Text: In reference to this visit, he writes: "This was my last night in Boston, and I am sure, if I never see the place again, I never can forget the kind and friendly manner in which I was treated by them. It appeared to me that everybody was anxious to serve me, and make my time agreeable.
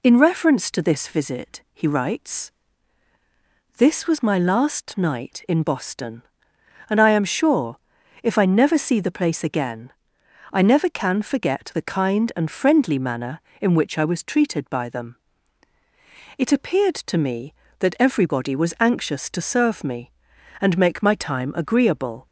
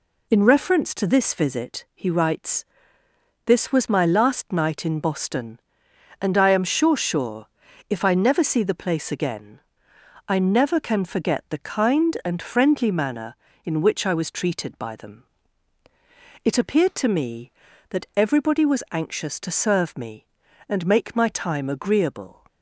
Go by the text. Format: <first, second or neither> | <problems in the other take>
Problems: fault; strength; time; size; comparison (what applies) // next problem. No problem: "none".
first | says "sure" twice; at 6.9 s